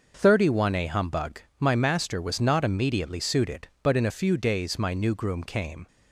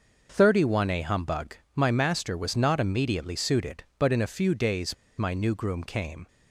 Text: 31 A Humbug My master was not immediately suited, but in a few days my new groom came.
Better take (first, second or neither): first